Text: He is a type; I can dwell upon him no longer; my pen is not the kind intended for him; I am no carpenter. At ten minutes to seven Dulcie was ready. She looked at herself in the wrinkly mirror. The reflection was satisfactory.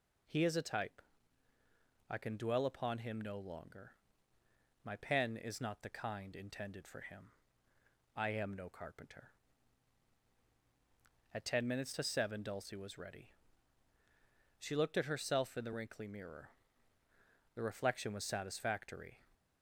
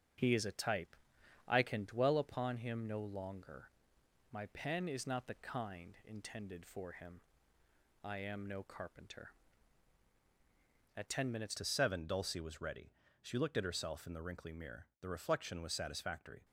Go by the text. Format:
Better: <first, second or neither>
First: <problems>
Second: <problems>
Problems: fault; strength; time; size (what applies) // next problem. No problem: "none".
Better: first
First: none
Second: starts louder than the rest; until 1.6 s; 7 dB // changes voice at "to"; from 11.5 s on; 4.9 s long